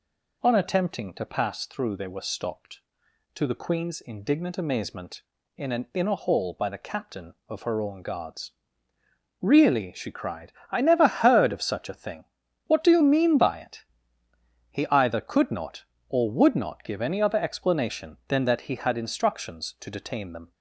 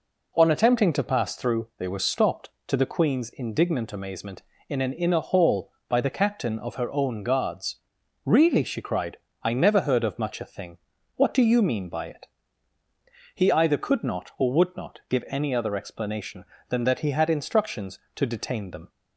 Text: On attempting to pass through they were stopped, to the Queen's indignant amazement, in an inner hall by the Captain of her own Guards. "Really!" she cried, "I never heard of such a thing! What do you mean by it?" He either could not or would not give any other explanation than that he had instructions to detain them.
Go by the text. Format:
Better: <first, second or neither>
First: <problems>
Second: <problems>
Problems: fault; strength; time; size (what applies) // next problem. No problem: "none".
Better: first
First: none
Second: says "much" for "such"; at 10.1 s